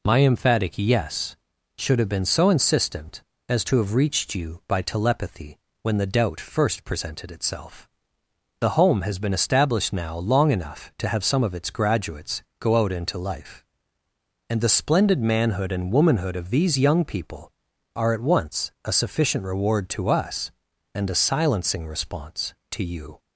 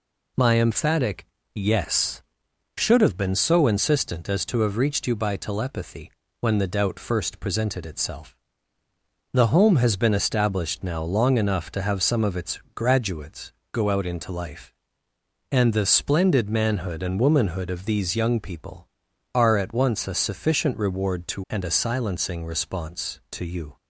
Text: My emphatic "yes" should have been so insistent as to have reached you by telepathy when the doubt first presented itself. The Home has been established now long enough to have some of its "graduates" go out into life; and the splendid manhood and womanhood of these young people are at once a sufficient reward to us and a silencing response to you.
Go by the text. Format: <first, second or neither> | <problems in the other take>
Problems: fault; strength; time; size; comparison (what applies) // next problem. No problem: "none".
first | pauses between "emphatic" and "yes"; slight; at 1.2 s; 0.28 s long // pauses between "telepathy" and "when"; slight; at 6.1 s; 0.30 s long; slight in the first // pauses between "its" and "graduates"; slight; at 12.5 s; 0.16 s long // pauses between "graduates" and "go"; slight; at 13.5 s; 0.18 s long; slight in the first // skips "us"; at 21.4 s